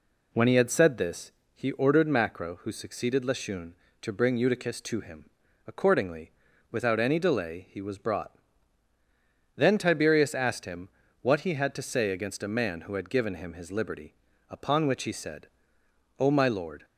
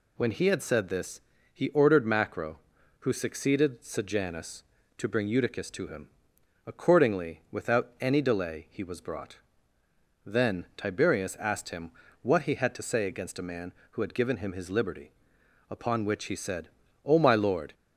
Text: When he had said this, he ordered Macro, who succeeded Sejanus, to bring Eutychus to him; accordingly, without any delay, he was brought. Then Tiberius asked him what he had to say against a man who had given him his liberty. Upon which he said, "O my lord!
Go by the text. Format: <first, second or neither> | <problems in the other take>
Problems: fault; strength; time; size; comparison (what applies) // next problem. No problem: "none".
second | says "Lashun" for "Sejanus"; at 3.2 s // pauses between "him" and "what"; slight; at 10.8 s; 0.32 s long; slight in the second